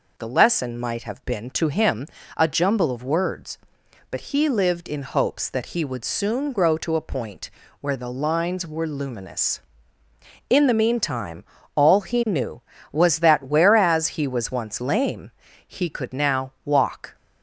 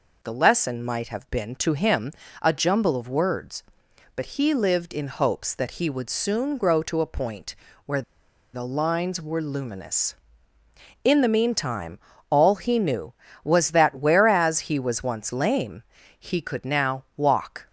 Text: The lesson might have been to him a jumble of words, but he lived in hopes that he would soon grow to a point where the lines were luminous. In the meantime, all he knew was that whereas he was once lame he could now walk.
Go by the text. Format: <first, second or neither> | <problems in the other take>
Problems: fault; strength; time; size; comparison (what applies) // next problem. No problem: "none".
first | pauses between "him" and "a"; slight; at 2.1 s; 0.30 s long; slight in the first // pauses between "point" and "where"; slight; at 7.5 s; 0.30 s long; slight in the first // pauses between "where" and "the"; noticeable; at 8.0 s; 0.51 s long // pauses between "lame" and "he"; slight; at 15.8 s; 0.34 s long; slight in the first